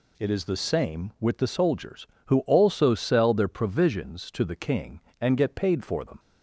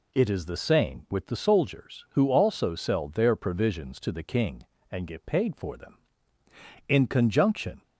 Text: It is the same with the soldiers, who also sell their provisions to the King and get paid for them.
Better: first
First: none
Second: goes on to say "In conjunction"; noticeable; from 6.8 s on; 0.94 s long

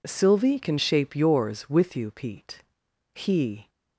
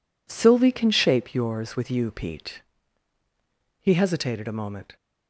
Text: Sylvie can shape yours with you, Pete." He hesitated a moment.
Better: second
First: stops before "hesitated a moment"; at 3.6 s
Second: none

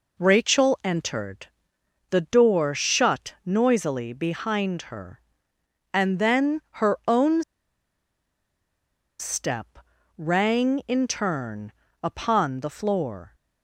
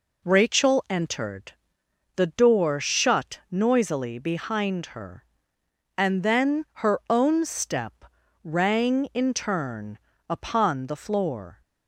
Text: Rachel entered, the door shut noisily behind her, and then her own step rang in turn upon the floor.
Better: second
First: pauses between "then" and "her"; slight; at 6.6 s; 0.20 s long // pauses between "own" and "step"; strong; at 7.4 s; 1.7 s long // pauses between "step" and "rang"; at 9.7 s; 0.40 s long // pauses between "turn" and "upon"; slight; at 11.7 s; 0.32 s long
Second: pauses between "then" and "her"; slight; at 6.6 s; 0.18 s long // pauses between "step" and "rang"; at 8.0 s; 0.40 s long // pauses between "turn" and "upon"; slight; at 9.9 s; 0.32 s long

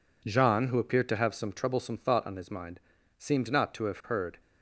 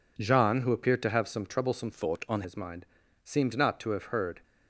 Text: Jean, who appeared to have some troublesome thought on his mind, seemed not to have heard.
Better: first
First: none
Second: changes voice from "thought" to "on"; from 1.9 to 2.4 s; 0.5 s long

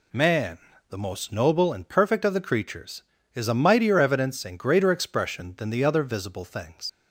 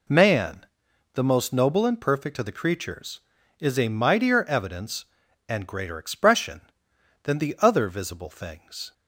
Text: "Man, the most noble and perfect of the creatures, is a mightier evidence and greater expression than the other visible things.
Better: second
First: leaves "things" unfinished; at 6.8 s; 65 ms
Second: none

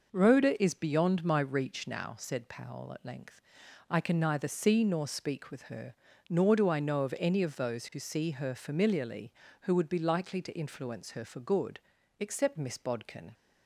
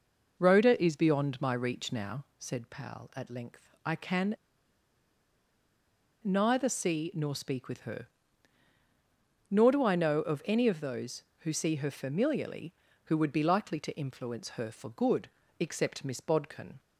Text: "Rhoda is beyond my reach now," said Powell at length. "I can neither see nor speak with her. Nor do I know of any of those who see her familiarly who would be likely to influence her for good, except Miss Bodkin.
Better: first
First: none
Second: pauses between "can" and "neither"; strong; at 4.3 s; 1.8 s long

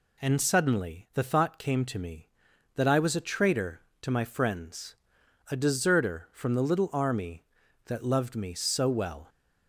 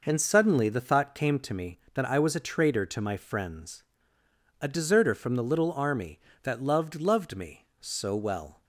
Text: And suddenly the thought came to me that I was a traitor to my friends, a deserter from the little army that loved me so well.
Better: first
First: none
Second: says "loved" twice; at 6.9 s

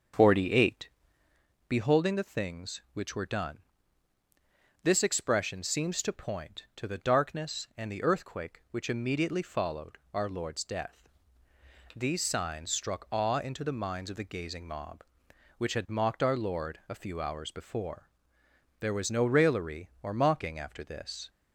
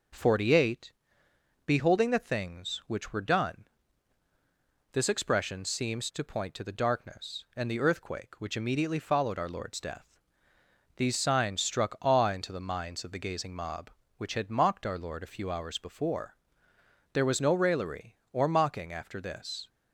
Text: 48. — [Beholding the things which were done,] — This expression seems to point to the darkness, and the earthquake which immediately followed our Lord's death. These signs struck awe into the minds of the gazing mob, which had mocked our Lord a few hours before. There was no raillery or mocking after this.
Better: second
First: starts louder than the rest; until 1.4 s; 7 dB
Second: none

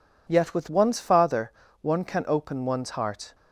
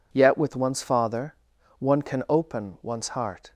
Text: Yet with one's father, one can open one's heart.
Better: neither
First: none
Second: none

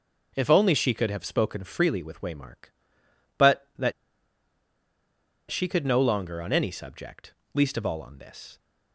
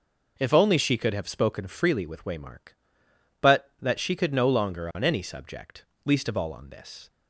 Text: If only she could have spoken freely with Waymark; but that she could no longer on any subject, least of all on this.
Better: second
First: pauses between "that" and "she"; strong; at 3.9 s; 1.5 s long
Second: none

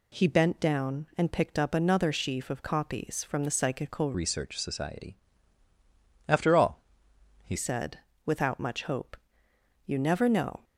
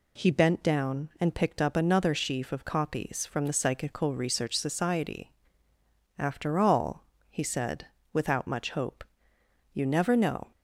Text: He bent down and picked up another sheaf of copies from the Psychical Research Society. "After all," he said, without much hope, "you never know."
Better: second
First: changes voice from "Research" to "he"; from 4.1 to 7.5 s; 3.4 s long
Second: none

